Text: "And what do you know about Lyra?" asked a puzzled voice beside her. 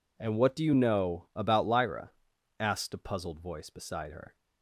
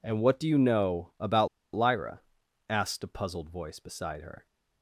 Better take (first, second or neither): first